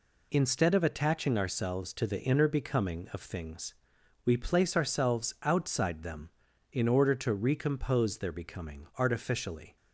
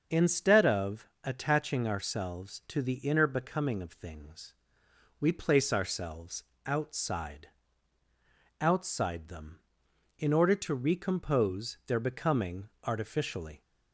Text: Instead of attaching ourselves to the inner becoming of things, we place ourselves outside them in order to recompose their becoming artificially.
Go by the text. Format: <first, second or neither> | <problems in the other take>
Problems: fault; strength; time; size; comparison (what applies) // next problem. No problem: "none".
first | starts louder than the rest; until 1.2 s; 6.5 dB // pauses between "of" and "attaching"; slight; at 1.0 s; 0.16 s long // pauses between "ourselves" and "outside"; slight; at 6.4 s; 0.20 s long // says "outside" twice; at 8.5 s // pauses between "becoming" and "artificially"; slight; at 12.6 s; 0.16 s long